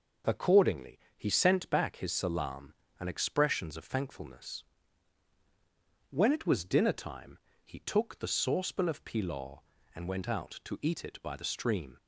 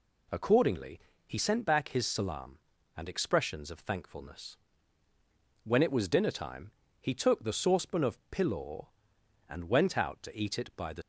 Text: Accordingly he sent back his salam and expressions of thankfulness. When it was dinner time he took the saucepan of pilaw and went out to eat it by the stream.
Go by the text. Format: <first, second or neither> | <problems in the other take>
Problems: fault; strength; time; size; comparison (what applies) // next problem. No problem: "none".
first | pauses between "Accordingly" and "he"; slight; at 1.0 s; 0.26 s long; slight in the first // pauses between "time" and "he"; slight; at 6.7 s; 0.28 s long; slight in the first // stops before "stream"; at 11.0 s